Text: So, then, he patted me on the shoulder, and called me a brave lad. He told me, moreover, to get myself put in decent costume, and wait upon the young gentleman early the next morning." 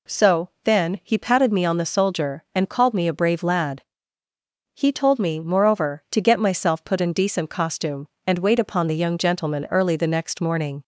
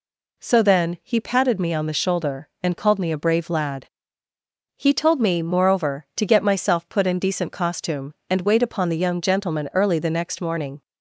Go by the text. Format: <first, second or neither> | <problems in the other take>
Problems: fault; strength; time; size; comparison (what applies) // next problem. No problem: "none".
second | says "soldier" for "shoulder"; at 1.8 s